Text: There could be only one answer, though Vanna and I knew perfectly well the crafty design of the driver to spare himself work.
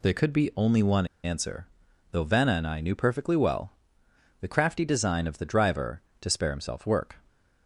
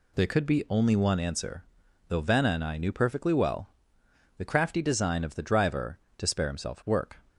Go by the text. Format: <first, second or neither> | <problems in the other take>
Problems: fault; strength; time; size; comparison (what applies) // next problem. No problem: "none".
second | pauses between "one" and "answer"; slight; at 1.0 s; 0.18 s long // pauses between "well" and "the"; noticeable; at 3.7 s; 0.66 s long; noticeable in the second